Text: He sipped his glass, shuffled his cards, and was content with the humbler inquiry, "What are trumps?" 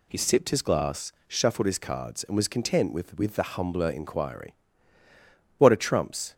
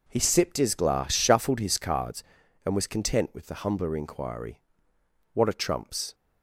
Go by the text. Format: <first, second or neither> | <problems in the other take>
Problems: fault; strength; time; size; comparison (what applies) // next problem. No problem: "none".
second | says "with" twice; at 3.1 s